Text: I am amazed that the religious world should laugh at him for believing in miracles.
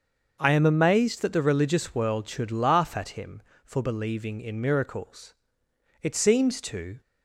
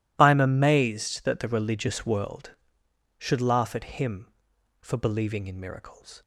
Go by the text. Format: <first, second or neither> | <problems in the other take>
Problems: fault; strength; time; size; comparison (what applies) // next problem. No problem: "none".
second | starts louder than the rest; until 1.4 s; 6.5 dB // goes on to say "It seems to"; noticeable; from 6.0 s on; 0.98 s long